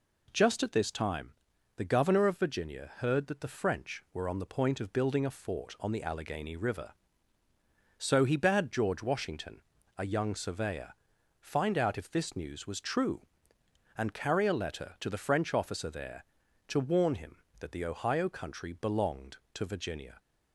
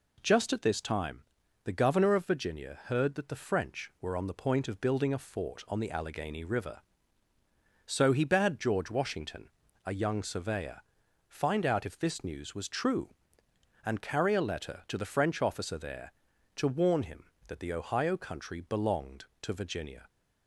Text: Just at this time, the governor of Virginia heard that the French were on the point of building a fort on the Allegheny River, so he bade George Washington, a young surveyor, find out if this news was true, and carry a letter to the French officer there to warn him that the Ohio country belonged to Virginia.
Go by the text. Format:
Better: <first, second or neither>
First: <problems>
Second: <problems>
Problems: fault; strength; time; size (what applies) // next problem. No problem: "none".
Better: neither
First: none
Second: none